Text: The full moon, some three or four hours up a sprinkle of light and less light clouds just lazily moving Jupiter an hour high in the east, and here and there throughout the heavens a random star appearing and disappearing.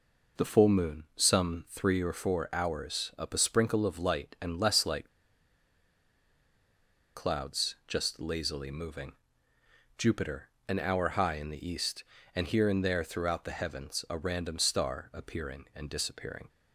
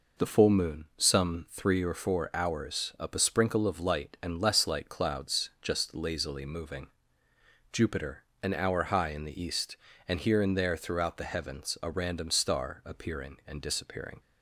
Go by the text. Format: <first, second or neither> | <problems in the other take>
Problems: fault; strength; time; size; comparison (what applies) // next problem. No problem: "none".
second | pauses between "light" and "clouds"; strong; at 5.0 s; 2.0 s long // pauses between "moving" and "Jupiter"; noticeable; at 9.1 s; 0.84 s long; noticeable in the second // pauses between "Jupiter" and "an"; slight; at 10.4 s; 0.20 s long; slight in the second